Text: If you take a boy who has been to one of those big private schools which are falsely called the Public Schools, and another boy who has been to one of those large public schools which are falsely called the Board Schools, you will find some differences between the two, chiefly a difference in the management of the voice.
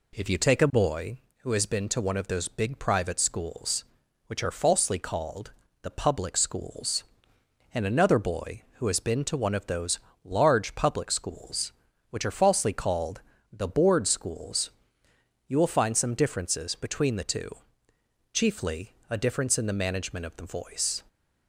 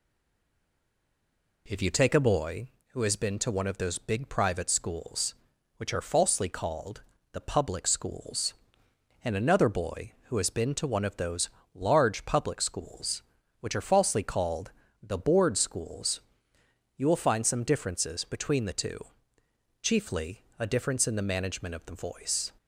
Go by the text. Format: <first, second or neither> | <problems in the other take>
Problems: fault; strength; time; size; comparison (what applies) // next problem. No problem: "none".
first | stays silent before the first word; noticeable; until 1.6 s; 1.6 s long // pauses between "called" and "the"; slight; at 7.0 s; 0.30 s long; slight in the first // pauses between "those" and "large"; slight; at 11.4 s; 0.26 s long; slight in the first // pauses between "called" and "the"; slight; at 14.7 s; 0.32 s long; slight in the first // pauses between "chiefly" and "a"; slight; at 20.4 s; 0.18 s long; slight in the first